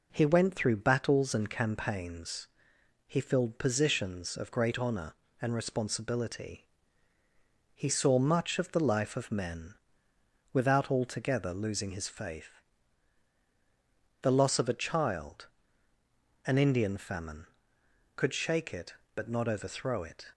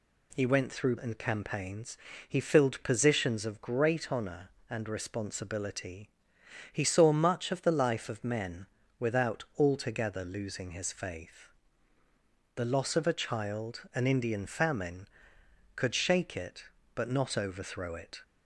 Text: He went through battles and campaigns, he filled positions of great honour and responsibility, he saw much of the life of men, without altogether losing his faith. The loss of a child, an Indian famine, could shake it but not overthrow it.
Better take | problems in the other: first | skips "battles"; at 0.9 s

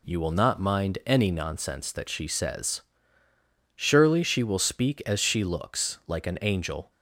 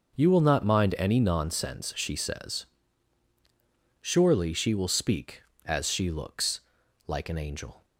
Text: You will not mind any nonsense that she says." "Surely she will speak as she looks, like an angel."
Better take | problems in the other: first | skips "that"; at 1.9 s

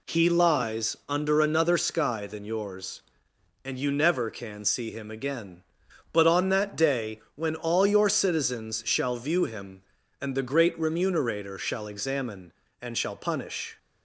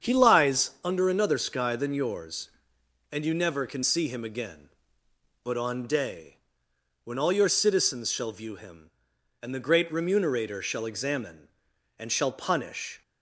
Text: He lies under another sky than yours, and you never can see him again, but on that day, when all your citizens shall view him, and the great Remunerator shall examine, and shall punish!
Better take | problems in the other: first | starts louder than the rest; strong; until 1.1 s; 7.5 dB // skips "that"; at 5.8 s

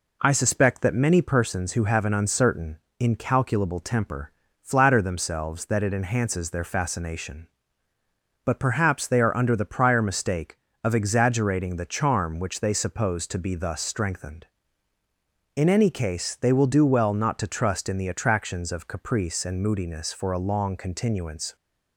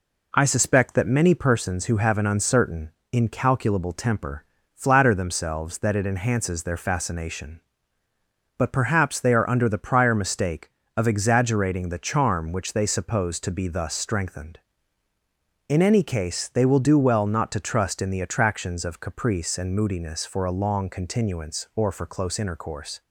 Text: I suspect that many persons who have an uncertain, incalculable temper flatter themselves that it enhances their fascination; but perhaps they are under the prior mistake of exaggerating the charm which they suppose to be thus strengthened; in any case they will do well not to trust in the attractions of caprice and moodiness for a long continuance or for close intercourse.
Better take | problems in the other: second | pauses between "temper" and "flatter"; slight; at 4.3 s; 0.28 s long; slight in the second // stops before "or for close intercourse"; at 21.5 s

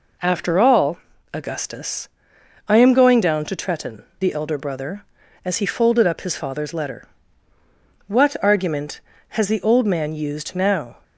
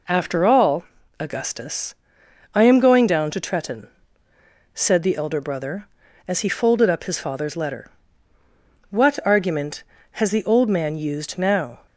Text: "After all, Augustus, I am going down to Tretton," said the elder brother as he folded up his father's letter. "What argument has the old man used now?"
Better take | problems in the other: second | skips "said"; at 4.1 s

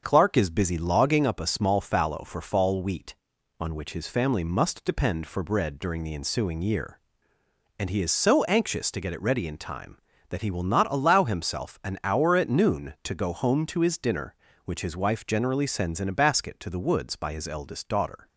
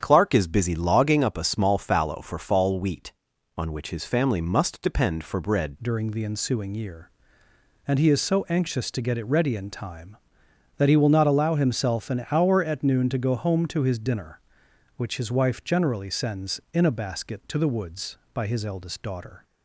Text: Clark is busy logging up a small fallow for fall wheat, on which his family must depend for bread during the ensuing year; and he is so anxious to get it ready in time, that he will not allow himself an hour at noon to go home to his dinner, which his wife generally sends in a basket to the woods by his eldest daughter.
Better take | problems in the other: first | starts louder than the rest; strong; until 1.0 s; 8.5 dB; also in the first // changes voice at "during"; from 5.8 s on; 13.6 s long

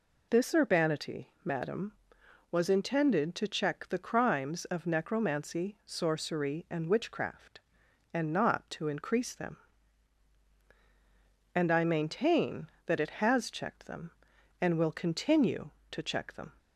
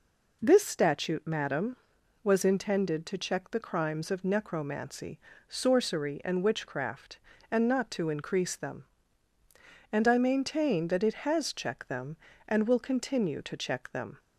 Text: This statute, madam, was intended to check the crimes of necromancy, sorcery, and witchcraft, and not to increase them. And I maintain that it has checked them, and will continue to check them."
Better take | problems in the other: second | says "urbanity" for "statute"; at 0.5 s

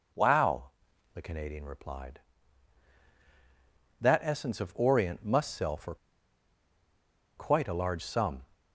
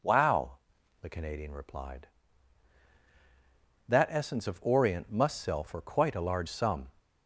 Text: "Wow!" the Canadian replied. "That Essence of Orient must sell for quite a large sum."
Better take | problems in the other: second | pauses between "for" and "quite"; strong; at 5.9 s; 1.4 s long

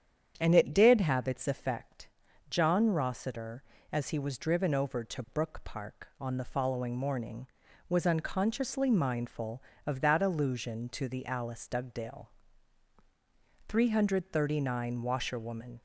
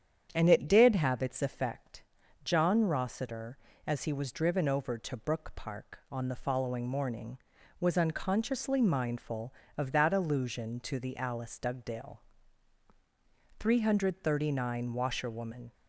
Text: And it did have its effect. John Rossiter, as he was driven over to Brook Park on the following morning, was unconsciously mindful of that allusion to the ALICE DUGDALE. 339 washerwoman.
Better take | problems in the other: neither | starts louder than the rest; strong; the same in both

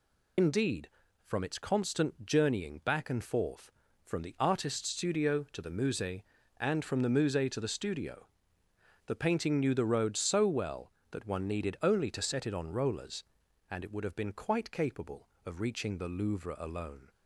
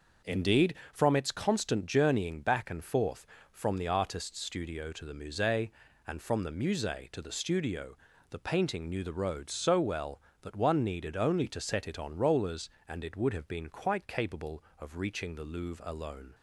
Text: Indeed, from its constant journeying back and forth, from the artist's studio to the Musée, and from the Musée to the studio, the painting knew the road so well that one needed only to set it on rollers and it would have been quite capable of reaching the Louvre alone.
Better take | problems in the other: second | loses the start of "Indeed"; at 0.3 s; 75 ms

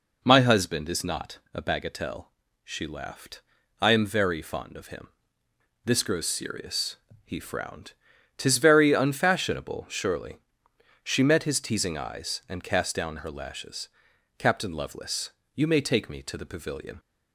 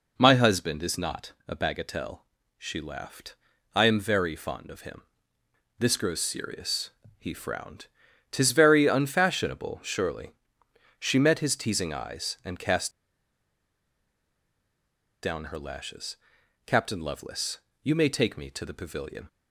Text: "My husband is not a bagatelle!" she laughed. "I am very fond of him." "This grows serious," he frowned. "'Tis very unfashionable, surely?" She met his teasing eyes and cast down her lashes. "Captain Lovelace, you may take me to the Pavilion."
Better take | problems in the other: first | pauses between "cast" and "down"; strong; at 12.8 s; 2.3 s long

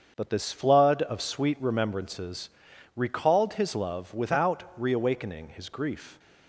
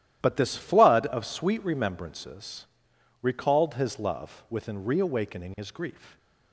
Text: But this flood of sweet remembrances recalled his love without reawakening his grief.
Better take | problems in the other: first | starts louder than the rest; strong; until 1.2 s; 12.5 dB; also in the first // pauses between "remembrances" and "recalled"; noticeable; at 2.6 s; 0.56 s long; noticeable in the first // says "within" for "without"; at 4.4 s

